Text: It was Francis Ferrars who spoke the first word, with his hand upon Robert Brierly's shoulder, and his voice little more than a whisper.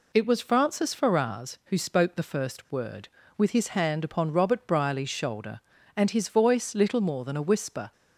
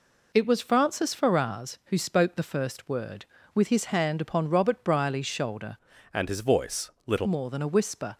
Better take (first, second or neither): first